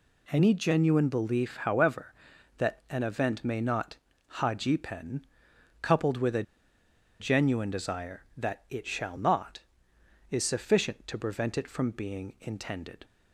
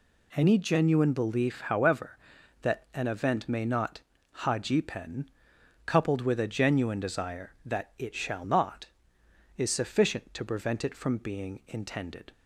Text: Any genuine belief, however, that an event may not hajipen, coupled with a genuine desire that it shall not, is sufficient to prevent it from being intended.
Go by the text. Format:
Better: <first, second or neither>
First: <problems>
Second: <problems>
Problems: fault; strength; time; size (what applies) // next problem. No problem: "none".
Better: second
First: pauses between "not" and "hajipen"; at 3.9 s; 0.40 s long // pauses between "a" and "genuine"; noticeable; at 6.4 s; 0.77 s long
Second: pauses between "not" and "hajipen"; at 4.0 s; 0.40 s long